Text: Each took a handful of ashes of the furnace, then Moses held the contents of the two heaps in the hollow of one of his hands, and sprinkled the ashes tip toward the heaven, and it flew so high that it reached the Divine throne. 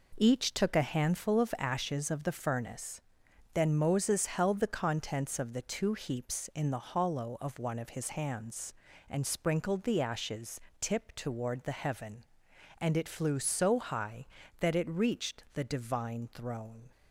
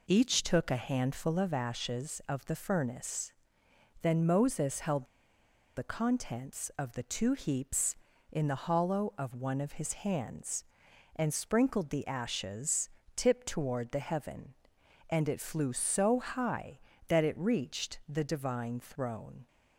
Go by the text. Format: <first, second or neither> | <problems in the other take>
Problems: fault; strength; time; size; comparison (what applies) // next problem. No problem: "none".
first | pauses between "held" and "the"; noticeable; at 5.0 s; 0.72 s long // pauses between "ashes" and "tip"; slight; at 12.8 s; 0.26 s long; slight in the first